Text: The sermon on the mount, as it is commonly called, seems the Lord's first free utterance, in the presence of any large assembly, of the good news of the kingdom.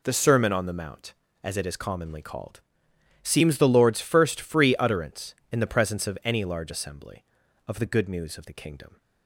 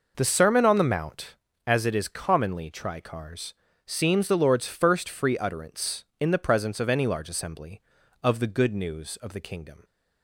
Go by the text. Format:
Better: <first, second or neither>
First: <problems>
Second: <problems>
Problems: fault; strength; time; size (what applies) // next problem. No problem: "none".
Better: first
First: none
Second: says "tricars" for "called"; at 2.7 s